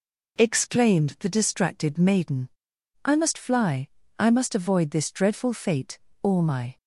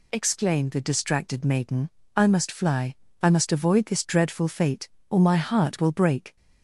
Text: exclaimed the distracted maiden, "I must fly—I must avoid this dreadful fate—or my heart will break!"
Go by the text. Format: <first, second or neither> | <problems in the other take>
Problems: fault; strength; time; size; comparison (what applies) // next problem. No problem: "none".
second | stops before "heart will break"; at 6.7 s